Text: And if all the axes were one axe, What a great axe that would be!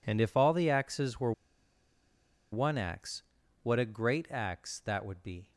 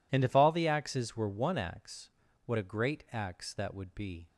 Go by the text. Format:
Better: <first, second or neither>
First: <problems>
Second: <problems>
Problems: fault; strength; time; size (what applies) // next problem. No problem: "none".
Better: second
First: pauses between "were" and "one"; at 1.3 s; 1.2 s long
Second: none